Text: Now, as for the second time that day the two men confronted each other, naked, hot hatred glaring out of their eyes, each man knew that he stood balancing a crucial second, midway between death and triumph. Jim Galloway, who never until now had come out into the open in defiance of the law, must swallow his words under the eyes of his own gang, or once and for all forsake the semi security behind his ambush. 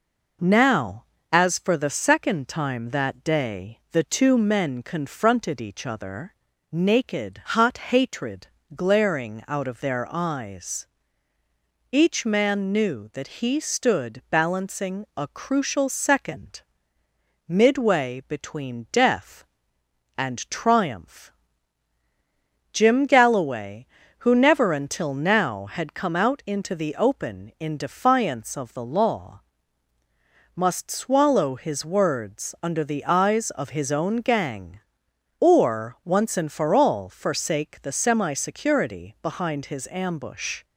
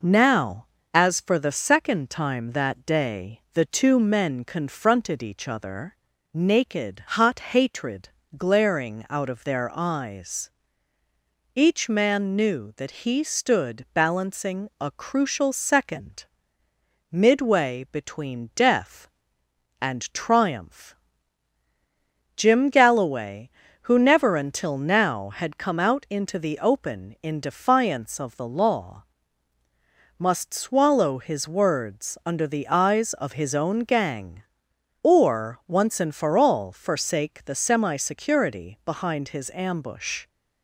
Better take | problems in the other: neither | pauses between "hatred" and "glaring"; slight; the same in both

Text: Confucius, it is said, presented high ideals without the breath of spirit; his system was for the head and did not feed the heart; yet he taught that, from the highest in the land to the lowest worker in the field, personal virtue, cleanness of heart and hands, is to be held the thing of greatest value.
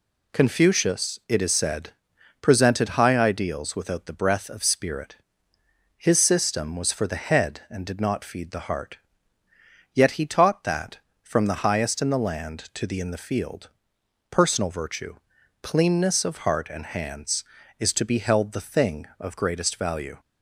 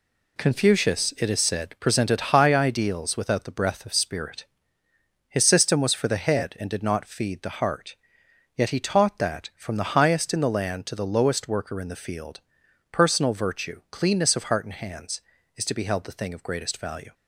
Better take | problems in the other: second | skips "lowest worker"; at 12.9 s

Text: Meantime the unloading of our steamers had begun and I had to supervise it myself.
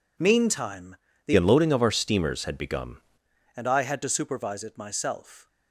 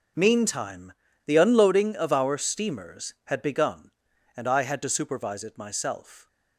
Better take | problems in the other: second | pauses between "Meantime" and "the"; slight; at 0.9 s; 0.32 s long; slight in the second // changes voice from "unloading" to "begun"; from 1.3 to 2.9 s; 1.6 s long

